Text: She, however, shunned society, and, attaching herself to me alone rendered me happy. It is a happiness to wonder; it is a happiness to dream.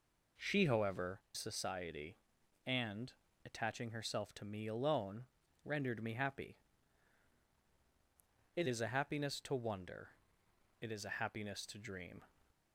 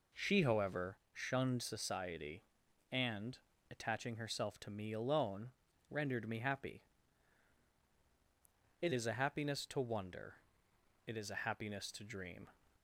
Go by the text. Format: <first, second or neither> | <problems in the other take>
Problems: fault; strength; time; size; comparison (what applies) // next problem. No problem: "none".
second | skips "shunned"; at 1.2 s // pauses between "alone" and "rendered"; slight; at 5.2 s; 0.36 s long; slight in the second